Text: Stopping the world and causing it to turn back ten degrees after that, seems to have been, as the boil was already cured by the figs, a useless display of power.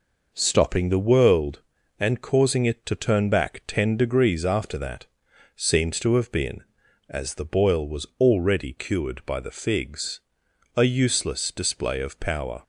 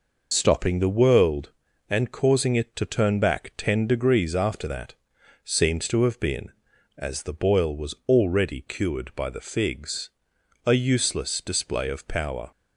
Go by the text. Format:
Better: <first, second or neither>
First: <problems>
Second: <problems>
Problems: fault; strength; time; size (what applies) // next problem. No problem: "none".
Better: first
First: none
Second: loses the start of "Stopping"; at 0.3 s; 70 ms